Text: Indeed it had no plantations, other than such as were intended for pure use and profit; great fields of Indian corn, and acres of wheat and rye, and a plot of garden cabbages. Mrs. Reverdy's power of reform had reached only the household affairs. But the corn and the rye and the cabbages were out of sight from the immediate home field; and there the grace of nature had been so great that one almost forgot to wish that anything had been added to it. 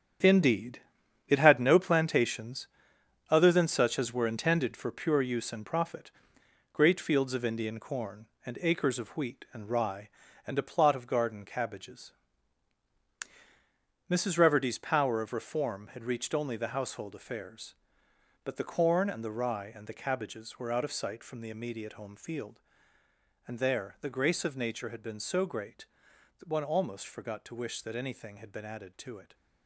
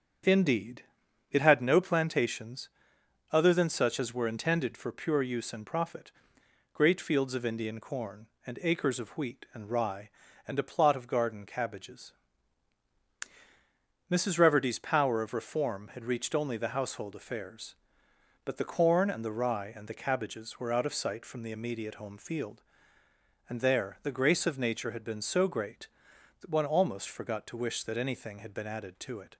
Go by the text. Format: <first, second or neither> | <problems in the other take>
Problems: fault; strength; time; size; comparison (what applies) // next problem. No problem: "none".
second | gets quieter; strong; throughout; 9.5 dB // starts louder than the rest; strong; until 1.7 s; 8.5 dB; strong in the second // pauses between "Indeed" and "it"; noticeable; at 0.7 s; 0.48 s long; noticeable in the second